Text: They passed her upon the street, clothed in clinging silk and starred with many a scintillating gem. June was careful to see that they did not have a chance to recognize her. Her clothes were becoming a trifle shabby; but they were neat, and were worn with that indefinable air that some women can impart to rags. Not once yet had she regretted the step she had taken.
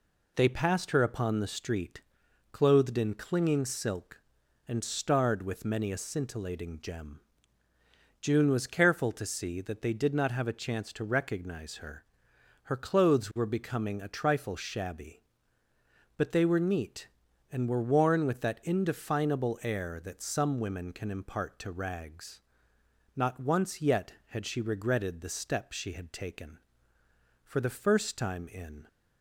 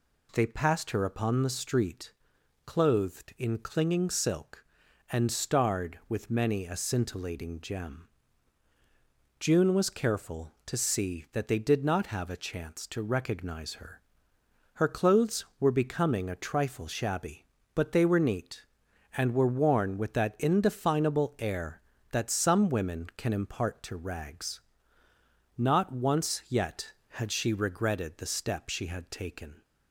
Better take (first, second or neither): second